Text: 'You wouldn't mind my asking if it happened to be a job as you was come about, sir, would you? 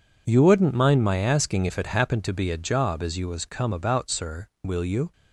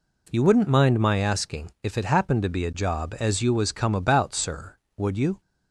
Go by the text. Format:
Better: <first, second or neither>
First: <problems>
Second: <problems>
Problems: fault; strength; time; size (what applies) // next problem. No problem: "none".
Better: second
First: says "will" for "would"; at 4.6 s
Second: none